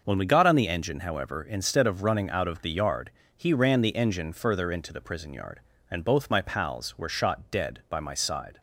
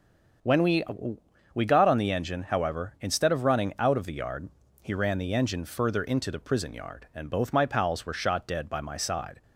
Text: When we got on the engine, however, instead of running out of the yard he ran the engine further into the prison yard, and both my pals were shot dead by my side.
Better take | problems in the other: first | starts louder than the rest; strong; until 2.1 s; 7 dB; also in the first // says "we" twice; at 1.5 s // pauses between "yard" and "he"; slight; at 4.4 s; 0.34 s long; slight in the first

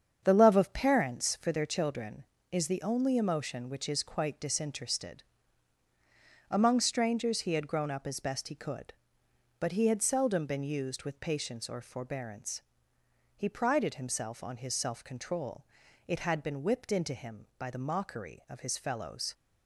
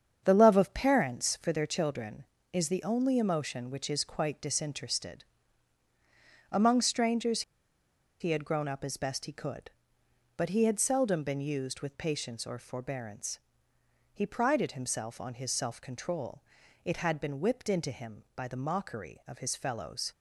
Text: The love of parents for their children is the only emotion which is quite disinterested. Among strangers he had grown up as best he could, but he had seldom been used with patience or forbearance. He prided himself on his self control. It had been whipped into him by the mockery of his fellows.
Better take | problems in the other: first | starts louder than the rest; strong; until 1.2 s; 7.5 dB; strong in the first // pauses between "strangers" and "he"; noticeable; at 7.4 s; 0.79 s long

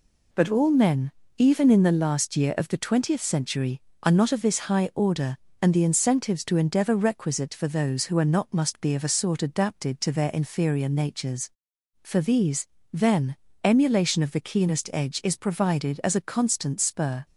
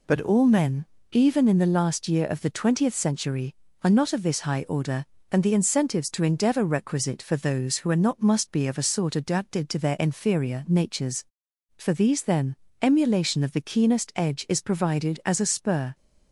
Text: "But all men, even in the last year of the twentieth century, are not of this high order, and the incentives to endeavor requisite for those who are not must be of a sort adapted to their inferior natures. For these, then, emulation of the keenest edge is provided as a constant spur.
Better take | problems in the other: first | skips "constant"; at 15.4 s

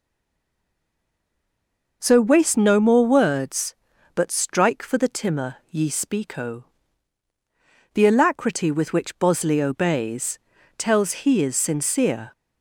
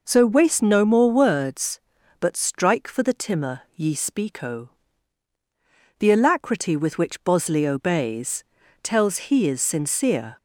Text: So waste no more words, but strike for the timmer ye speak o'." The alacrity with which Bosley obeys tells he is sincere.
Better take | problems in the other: second | stays silent before the first word; noticeable; until 2.0 s; 2.0 s long // pauses between "obeys" and "tells"; at 10.3 s; 0.40 s long; also in the second

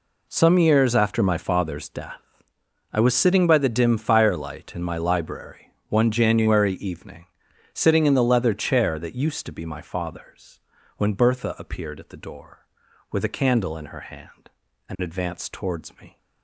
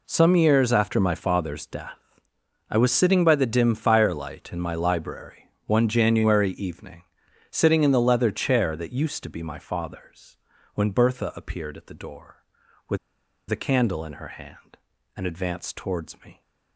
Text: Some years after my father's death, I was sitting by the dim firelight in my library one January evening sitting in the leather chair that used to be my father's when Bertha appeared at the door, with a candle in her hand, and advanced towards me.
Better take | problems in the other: first | pauses between "library" and "one"; slight; at 5.4 s; 0.16 s long; slight in the first // pauses between "evening" and "sitting"; at 7.0 s; 0.44 s long; also in the first // pauses between "father's" and "when"; at 10.3 s; 0.38 s long; also in the first // pauses between "with" and "a"; noticeable; at 12.9 s; 0.53 s long

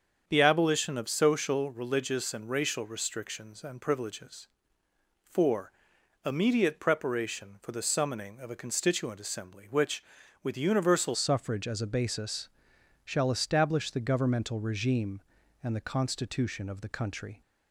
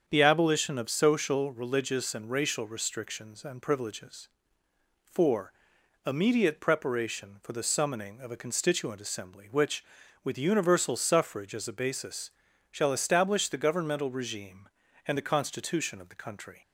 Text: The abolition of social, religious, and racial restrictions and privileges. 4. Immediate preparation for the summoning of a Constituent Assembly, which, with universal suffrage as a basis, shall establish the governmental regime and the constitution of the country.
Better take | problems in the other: second | starts louder than the rest; strong; until 1.2 s; 7.5 dB; strong in the second // changes voice at "suffrage"; from 11.1 s on; 6.3 s long

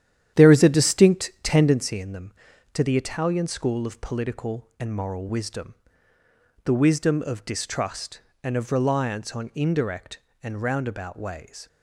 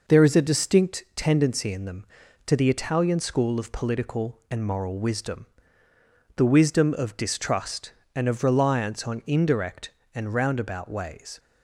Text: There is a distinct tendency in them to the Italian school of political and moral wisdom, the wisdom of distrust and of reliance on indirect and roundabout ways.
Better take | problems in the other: second | starts louder than the rest; strong; until 1.9 s; 10.5 dB

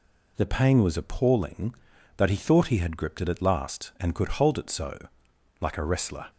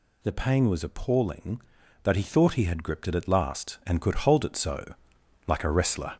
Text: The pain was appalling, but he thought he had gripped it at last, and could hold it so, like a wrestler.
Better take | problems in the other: first | gets louder; throughout; 6.5 dB

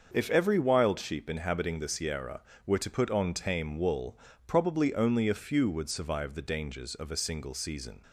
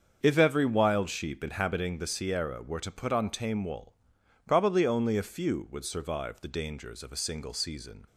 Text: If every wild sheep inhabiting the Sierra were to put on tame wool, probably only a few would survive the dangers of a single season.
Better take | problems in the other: neither | starts louder than the rest; the same in both

